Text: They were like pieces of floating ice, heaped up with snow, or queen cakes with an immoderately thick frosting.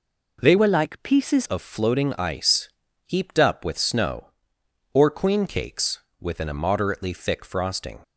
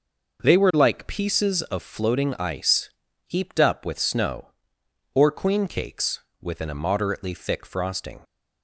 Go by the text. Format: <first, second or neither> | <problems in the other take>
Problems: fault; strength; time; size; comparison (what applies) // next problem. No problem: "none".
second | changes voice from "were" to "pieces"; from 0.5 to 1.4 s; 0.9 s long